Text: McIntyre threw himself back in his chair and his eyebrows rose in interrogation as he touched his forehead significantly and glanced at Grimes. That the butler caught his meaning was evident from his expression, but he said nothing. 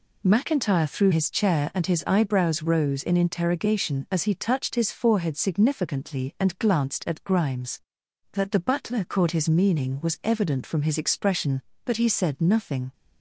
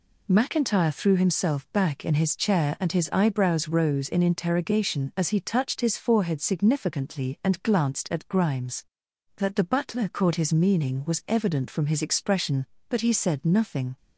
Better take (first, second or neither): second